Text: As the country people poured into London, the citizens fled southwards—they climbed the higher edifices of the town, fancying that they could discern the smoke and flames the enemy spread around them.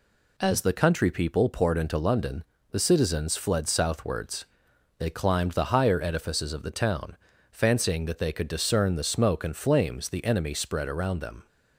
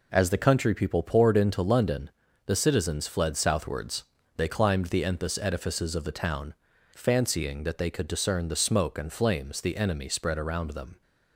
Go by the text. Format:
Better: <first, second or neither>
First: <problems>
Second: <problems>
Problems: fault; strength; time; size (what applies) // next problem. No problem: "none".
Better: first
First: none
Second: says "enthus" for "higher"; at 5.0 s